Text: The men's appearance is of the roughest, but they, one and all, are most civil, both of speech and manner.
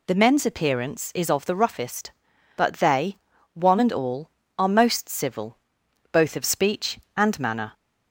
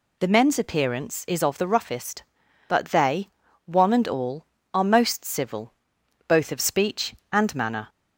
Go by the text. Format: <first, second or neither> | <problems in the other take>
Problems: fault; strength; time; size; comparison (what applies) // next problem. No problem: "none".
neither | none